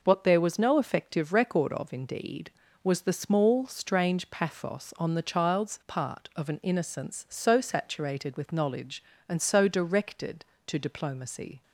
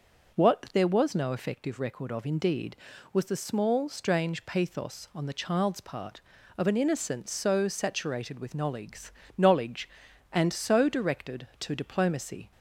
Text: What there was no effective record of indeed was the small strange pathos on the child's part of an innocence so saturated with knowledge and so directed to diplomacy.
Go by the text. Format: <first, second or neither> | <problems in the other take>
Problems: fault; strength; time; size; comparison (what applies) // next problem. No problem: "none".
first | says "knowledge" twice; at 9.3 s